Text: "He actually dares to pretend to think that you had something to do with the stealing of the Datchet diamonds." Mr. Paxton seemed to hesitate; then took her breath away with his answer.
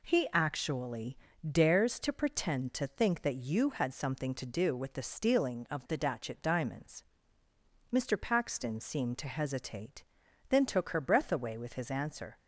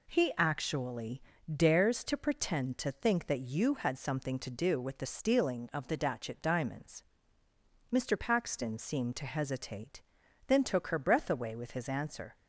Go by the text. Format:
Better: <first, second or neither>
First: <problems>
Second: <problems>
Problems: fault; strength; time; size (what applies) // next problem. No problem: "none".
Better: neither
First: pauses between "actually" and "dares"; slight; at 1.1 s; 0.32 s long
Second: pauses between "actually" and "dares"; slight; at 1.2 s; 0.32 s long